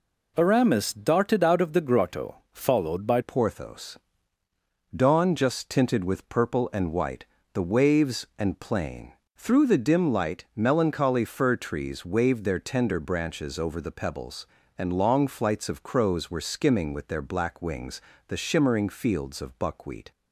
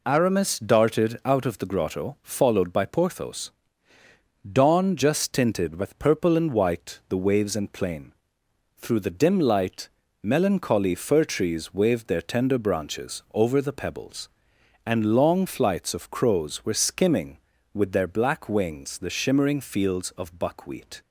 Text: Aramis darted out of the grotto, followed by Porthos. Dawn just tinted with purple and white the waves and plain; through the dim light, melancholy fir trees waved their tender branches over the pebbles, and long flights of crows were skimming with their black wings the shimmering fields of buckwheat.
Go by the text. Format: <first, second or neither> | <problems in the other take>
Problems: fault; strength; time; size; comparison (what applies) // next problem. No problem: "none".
second | changes voice at "Porthos"; from 3.2 s on; 16.9 s long // pauses between "white" and "the"; slight; at 7.2 s; 0.26 s long // pauses between "wings" and "the"; slight; at 18.0 s; 0.28 s long